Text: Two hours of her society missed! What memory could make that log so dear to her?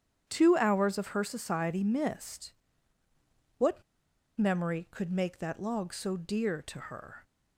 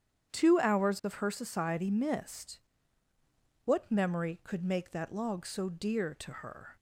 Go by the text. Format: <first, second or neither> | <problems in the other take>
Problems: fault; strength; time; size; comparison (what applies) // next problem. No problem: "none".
second | starts louder than the rest; strong; until 1.2 s; 9 dB; strong in the second // pauses between "What" and "memory"; noticeable; at 3.8 s; 0.54 s long